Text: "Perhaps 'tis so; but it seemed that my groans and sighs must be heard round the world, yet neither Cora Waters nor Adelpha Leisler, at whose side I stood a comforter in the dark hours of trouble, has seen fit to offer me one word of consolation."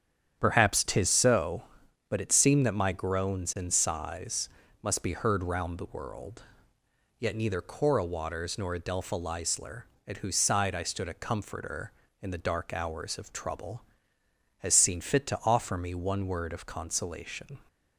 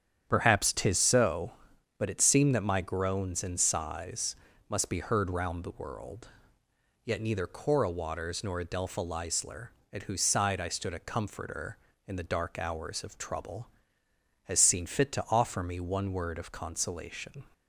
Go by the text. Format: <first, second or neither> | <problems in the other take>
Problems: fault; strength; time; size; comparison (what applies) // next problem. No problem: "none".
neither | starts louder than the rest; strong; the same in both // pauses between "sighs" and "must"; slight; the same in both